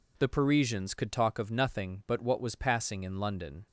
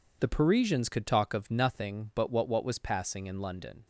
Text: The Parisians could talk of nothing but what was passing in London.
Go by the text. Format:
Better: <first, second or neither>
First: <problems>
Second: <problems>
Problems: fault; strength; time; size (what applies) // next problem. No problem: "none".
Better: first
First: none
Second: says "what" twice; at 2.4 s